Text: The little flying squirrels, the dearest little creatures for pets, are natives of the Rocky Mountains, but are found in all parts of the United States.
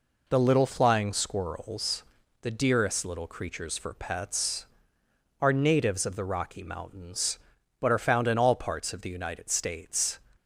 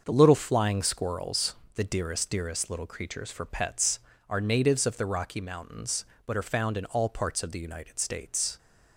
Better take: first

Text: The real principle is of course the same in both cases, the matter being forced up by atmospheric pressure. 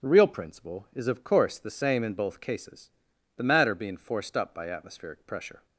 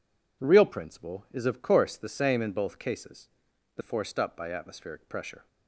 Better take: first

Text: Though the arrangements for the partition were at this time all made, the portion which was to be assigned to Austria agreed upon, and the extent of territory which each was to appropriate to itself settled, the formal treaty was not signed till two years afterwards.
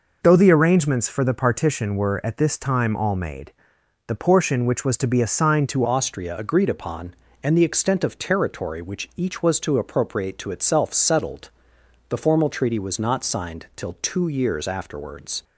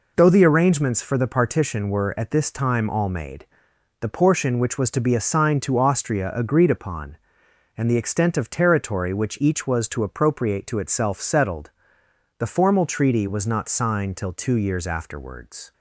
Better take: second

